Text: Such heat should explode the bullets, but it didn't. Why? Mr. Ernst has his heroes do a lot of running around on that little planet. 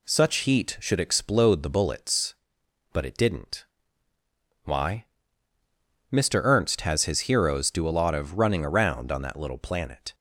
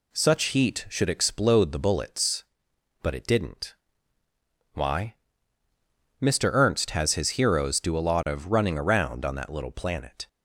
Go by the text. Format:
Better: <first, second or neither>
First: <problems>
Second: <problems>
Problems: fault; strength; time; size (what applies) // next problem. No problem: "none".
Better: neither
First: none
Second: none